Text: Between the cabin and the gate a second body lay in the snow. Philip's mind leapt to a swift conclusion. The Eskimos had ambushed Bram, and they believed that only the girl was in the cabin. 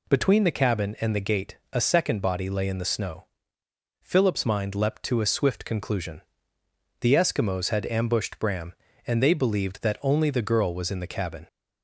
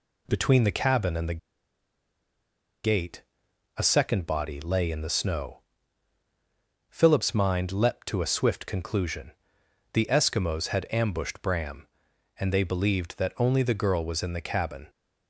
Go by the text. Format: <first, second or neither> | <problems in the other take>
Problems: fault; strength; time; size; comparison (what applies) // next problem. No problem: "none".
first | pauses between "the" and "gate"; strong; at 1.3 s; 1.4 s long // pauses between "gate" and "a"; noticeable; at 3.2 s; 0.56 s long; slight in the first